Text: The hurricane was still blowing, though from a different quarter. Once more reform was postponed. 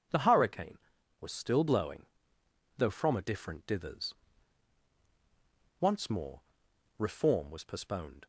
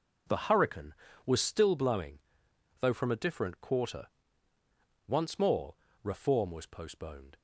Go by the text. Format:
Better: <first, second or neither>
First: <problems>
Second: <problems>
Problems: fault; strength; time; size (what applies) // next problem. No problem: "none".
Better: second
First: says "dithers" for "quarter"; at 3.6 s // pauses between "more" and "reform"; noticeable; at 6.4 s; 0.56 s long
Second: pauses between "more" and "reform"; slight; at 5.7 s; 0.28 s long